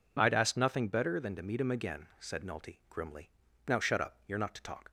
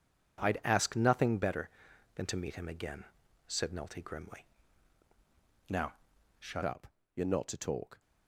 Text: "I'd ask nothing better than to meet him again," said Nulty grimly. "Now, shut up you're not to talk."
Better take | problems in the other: first | changes voice at "up"; from 6.6 s on; 1.3 s long // pauses between "up" and "you're"; slight; at 6.8 s; 0.26 s long

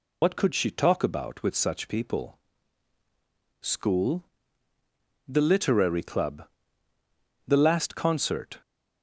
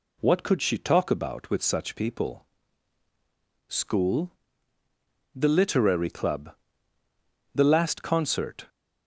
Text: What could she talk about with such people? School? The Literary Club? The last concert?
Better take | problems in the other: second | loses the start of "What"; at 0.2 s; 90 ms

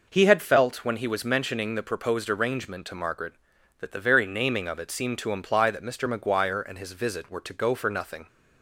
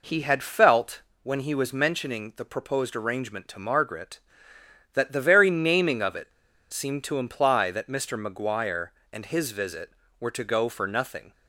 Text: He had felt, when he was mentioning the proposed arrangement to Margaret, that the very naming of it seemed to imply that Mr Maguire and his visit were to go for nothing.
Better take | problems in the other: first | pauses between "it" and "seemed"; at 6.3 s; 0.41 s long

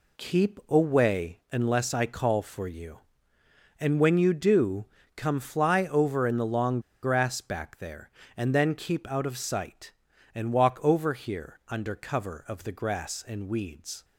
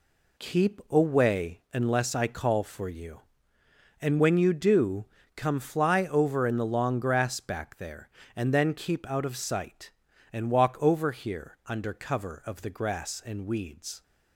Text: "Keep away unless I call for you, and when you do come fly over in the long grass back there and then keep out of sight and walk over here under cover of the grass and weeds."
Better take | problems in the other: second | pauses between "do" and "come"; slight; at 4.8 s; 0.32 s long; slight in the second // pauses between "long" and "grass"; slight; at 6.7 s; 0.23 s long

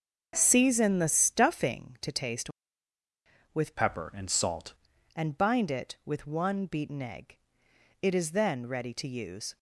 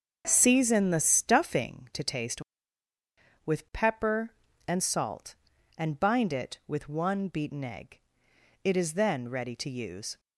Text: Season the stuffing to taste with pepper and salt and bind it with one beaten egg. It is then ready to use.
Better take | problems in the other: second | starts louder than the rest; until 1.3 s; 6.5 dB; noticeable in the second // changes voice from "pepper" to "salt"; from 3.7 to 4.7 s; 1.0 s long

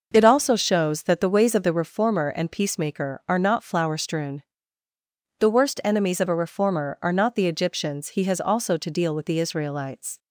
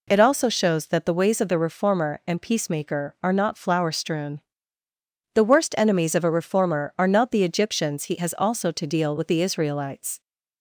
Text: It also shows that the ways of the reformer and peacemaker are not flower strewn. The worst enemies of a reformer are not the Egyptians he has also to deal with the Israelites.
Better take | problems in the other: neither | none

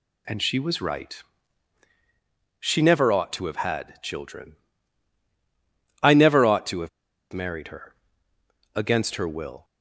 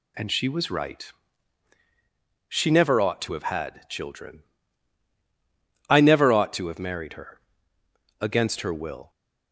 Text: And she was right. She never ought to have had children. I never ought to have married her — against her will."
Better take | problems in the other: second | pauses between "have" and "married"; at 6.8 s; 0.42 s long

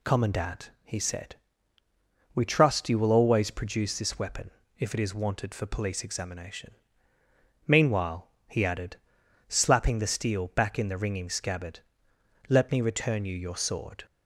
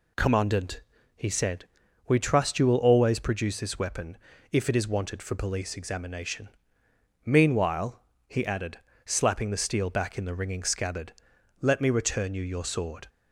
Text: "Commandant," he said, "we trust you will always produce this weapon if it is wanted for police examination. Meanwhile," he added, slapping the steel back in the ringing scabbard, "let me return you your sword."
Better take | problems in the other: neither | pauses between "weapon" and "if"; slight; the same in both

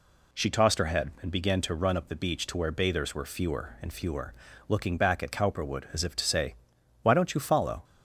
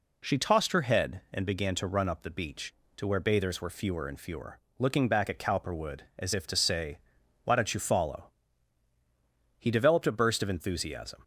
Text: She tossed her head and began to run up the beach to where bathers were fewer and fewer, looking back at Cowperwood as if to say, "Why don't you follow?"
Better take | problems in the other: first | goes on to say "He developed a burst of enthusiasm"; from 9.5 s on; 1.6 s long

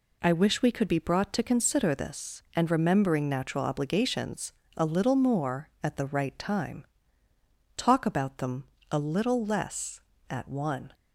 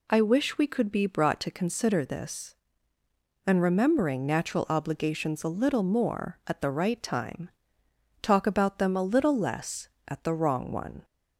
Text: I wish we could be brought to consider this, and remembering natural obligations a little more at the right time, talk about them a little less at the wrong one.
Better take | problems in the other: second | pauses between "obligations" and "a"; slight; at 4.5 s; 0.26 s long // pauses between "them" and "a"; slight; at 8.6 s; 0.26 s long // skips "the wrong"; at 10.4 s

